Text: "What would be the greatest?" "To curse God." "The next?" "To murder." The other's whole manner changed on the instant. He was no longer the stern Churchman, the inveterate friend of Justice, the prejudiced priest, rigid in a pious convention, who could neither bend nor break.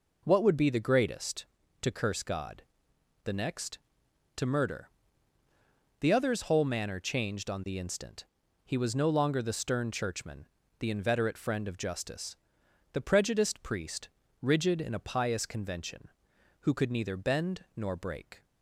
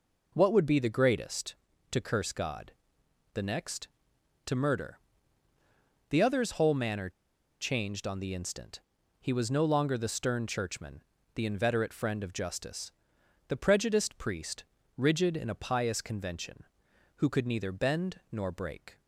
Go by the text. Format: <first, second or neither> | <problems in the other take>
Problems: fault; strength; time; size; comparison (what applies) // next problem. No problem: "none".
first | pauses between "manner" and "changed"; noticeable; at 7.1 s; 0.49 s long